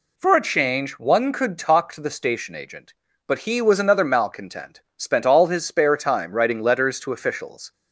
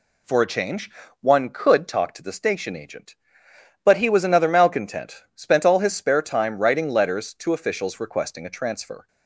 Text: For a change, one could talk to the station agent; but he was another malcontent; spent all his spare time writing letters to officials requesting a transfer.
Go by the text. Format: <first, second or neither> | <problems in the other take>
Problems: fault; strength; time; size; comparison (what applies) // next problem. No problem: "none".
second | stops before "requesting a transfer"; at 7.7 s